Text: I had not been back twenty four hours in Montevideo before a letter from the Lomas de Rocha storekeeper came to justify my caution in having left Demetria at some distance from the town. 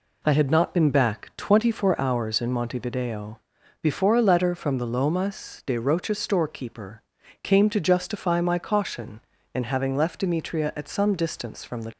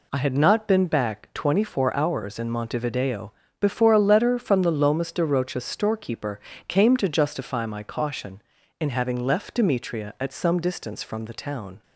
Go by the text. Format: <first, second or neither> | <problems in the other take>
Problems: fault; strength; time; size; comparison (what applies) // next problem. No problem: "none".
second | pauses between "Montevideo" and "before"; at 3.3 s; 0.42 s long; slight in the second // pauses between "storekeeper" and "came"; at 7.0 s; 0.40 s long; slight in the second // stops before "town"; at 11.9 s